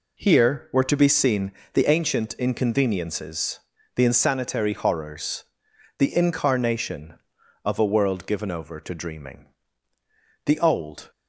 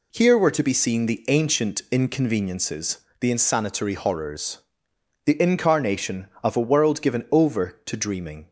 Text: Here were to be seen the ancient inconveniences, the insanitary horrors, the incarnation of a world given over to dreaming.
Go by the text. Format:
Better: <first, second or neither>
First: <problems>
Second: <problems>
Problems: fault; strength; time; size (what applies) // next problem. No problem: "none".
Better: second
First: pauses between "seen" and "the"; slight; at 1.5 s; 0.22 s long // goes on to say "The old"; noticeable; from 10.4 s on; 0.64 s long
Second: none